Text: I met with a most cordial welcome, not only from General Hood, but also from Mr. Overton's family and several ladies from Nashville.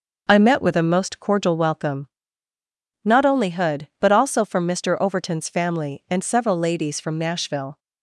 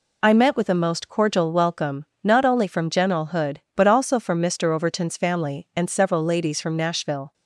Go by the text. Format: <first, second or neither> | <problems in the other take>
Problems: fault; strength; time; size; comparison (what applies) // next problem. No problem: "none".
second | skips "from General"; at 3.5 s